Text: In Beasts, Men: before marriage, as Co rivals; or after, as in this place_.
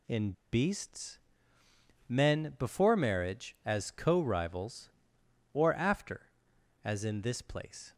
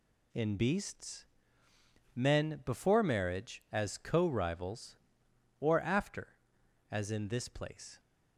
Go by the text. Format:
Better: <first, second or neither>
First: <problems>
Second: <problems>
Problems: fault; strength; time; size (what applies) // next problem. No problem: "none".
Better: second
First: pauses between "In" and "Beasts"; slight; at 0.3 s; 0.20 s long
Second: none